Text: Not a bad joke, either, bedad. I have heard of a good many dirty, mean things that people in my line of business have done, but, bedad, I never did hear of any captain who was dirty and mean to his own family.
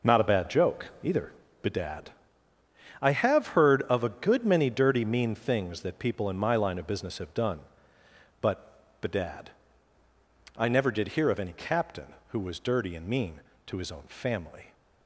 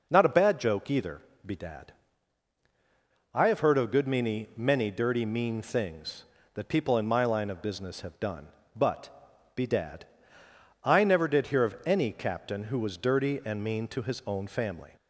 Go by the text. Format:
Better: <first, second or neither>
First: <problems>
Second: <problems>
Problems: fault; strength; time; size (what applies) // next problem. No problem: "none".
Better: first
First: none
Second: says "many" twice; at 4.5 s